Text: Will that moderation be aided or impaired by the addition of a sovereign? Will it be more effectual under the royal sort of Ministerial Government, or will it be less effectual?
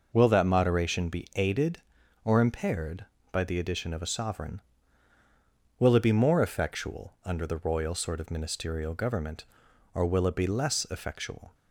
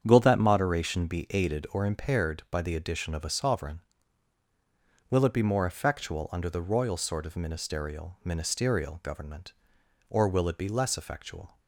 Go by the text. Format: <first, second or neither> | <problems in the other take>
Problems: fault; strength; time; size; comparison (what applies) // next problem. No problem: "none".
first | starts louder than the rest; strong; until 1.0 s; 8 dB // says "Ministerial" twice; at 8.2 s